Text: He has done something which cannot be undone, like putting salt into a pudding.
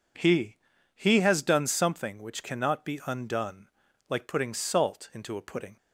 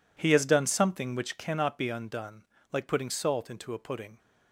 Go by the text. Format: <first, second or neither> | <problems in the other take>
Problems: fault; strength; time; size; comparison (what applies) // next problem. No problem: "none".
second | says "He" twice; at 0.9 s